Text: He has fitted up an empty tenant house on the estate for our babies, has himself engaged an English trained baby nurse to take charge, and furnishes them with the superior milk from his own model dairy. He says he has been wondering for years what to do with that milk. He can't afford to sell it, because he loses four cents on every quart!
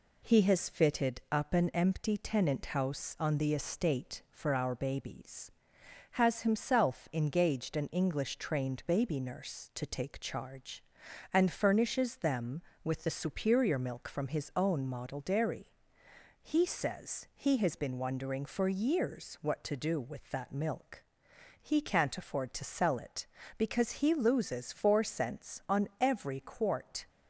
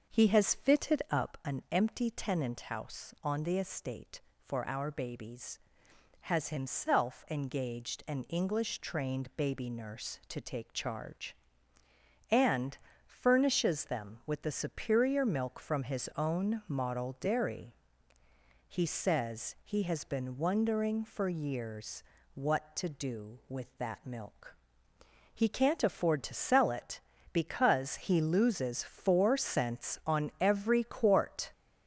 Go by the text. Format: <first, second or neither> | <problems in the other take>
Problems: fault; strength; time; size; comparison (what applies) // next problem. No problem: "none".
first | starts louder than the rest; until 1.3 s; 6 dB // pauses between "and" and "furnishes"; slight; at 12.7 s; 0.28 s long // pauses between "years" and "what"; slight; at 22.0 s; 0.30 s long